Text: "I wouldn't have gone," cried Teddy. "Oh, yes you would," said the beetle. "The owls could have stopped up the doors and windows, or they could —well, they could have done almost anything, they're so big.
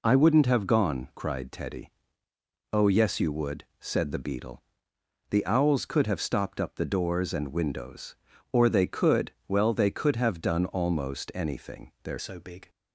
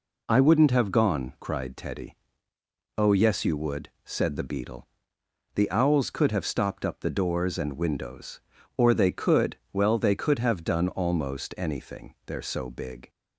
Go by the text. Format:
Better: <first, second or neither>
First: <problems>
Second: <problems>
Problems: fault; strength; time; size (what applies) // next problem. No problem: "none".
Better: second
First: changes voice at "so"; from 12.1 s on; 0.5 s long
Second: none